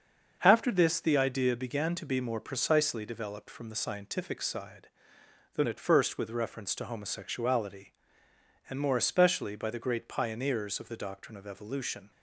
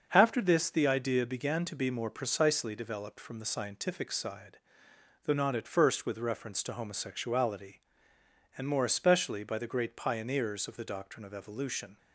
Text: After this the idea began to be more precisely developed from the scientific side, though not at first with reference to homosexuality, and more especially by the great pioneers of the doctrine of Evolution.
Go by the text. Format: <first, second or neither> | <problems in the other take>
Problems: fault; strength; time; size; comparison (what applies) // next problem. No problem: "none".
second | starts louder than the rest; until 1.4 s; 6.5 dB; also in the second // skips "not"; at 5.6 s